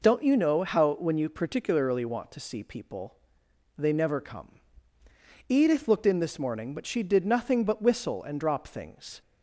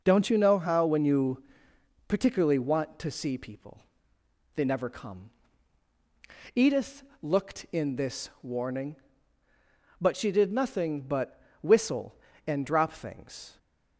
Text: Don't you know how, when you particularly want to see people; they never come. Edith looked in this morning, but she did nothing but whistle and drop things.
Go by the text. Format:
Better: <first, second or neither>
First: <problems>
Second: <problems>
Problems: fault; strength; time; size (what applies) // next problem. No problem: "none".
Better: first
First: none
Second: pauses between "you" and "particularly"; noticeable; at 1.4 s; 0.66 s long // pauses between "Edith" and "looked"; slight; at 7.0 s; 0.18 s long // says "warning" for "morning"; at 8.4 s // pauses between "but" and "whistle"; slight; at 11.3 s; 0.22 s long